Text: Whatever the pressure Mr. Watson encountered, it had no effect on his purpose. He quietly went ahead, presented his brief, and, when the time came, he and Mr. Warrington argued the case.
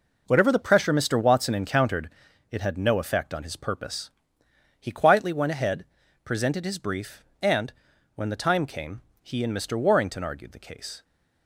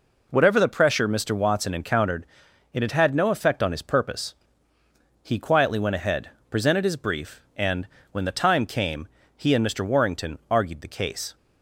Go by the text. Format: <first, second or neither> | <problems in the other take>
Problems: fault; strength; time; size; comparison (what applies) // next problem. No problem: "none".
first | says "had" twice; at 2.9 s